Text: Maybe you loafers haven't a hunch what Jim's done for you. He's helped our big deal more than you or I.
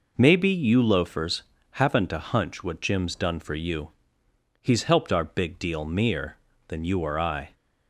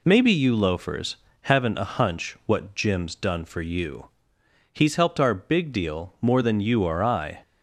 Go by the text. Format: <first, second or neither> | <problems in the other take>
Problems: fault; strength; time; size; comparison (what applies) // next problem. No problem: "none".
second | pauses between "loafers" and "haven't"; slight; at 1.4 s; 0.28 s long; slight in the second // says "mere" for "more"; at 5.8 s